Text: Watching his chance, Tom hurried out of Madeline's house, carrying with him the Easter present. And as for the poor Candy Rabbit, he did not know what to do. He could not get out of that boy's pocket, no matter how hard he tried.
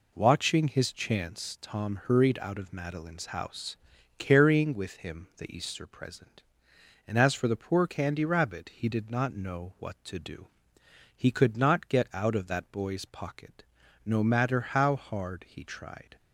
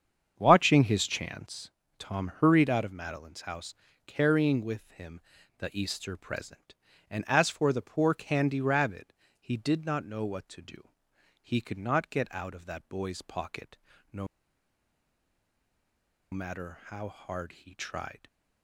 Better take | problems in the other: first | starts louder than the rest; strong; until 1.3 s; 7.5 dB // pauses between "him" and "the"; at 5.2 s; 0.38 s long // pauses between "no" and "matter"; strong; at 14.2 s; 2.0 s long

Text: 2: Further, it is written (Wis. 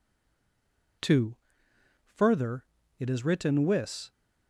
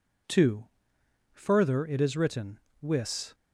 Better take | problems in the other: second | stays silent before the first word; until 1.0 s; 1.0 s long

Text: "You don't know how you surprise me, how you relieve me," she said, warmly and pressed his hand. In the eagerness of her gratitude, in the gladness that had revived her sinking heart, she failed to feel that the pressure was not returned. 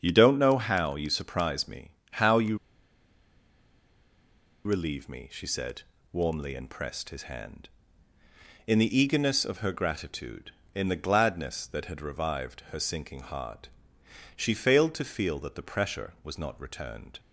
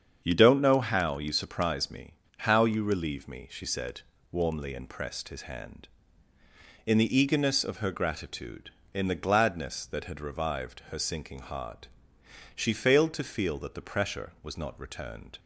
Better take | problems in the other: second | starts louder than the rest; strong; until 1.0 s; 7.5 dB; strong in the second // pauses between "you" and "relieve"; strong; at 2.5 s; 2.0 s long

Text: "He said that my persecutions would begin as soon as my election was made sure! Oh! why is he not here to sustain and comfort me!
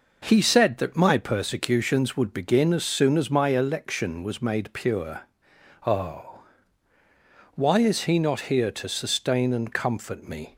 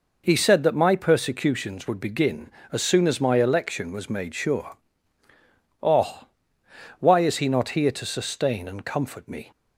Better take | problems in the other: second | says "pure" for "sure"; at 4.7 s

